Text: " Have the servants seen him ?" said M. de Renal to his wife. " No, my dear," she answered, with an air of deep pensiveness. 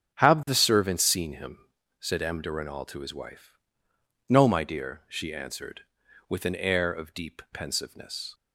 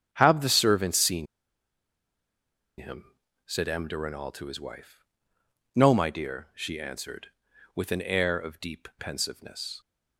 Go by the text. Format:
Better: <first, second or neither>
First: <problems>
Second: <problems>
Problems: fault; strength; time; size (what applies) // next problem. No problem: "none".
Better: first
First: starts louder than the rest; strong; until 1.1 s; 8 dB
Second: starts louder than the rest; strong; until 1.1 s; 8 dB // pauses between "seen" and "him"; strong; at 1.2 s; 1.5 s long